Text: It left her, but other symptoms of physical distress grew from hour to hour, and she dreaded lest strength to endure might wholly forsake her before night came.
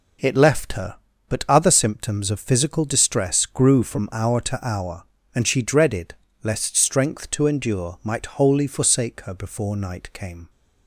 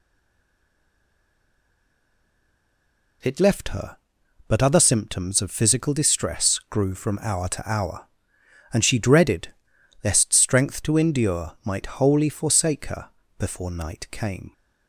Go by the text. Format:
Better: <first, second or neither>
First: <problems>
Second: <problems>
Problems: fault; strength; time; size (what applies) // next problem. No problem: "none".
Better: first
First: pauses between "dreaded" and "lest"; slight; at 6.1 s; 0.30 s long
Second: stays silent before the first word; strong; until 3.2 s; 3.2 s long // pauses between "dreaded" and "lest"; noticeable; at 9.4 s; 0.56 s long // pauses between "her" and "before"; slight; at 13.0 s; 0.28 s long